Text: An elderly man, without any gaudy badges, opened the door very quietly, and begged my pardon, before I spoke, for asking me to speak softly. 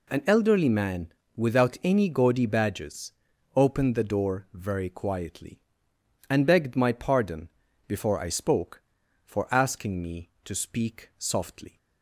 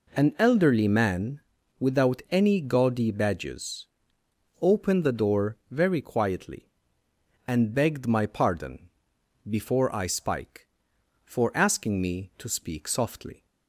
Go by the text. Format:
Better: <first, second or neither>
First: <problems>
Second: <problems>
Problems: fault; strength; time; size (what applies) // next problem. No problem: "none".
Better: first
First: none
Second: says "spike" for "spoke"; at 10.0 s